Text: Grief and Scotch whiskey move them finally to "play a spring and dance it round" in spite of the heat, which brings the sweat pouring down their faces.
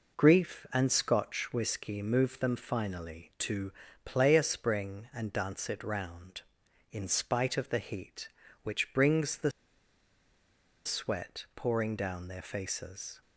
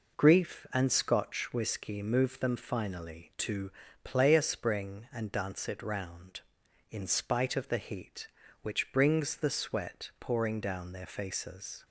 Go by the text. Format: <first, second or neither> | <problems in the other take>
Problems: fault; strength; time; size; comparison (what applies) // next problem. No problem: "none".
second | pauses between "to" and "play"; slight; at 3.7 s; 0.32 s long; slight in the second // pauses between "the" and "sweat"; strong; at 9.5 s; 1.3 s long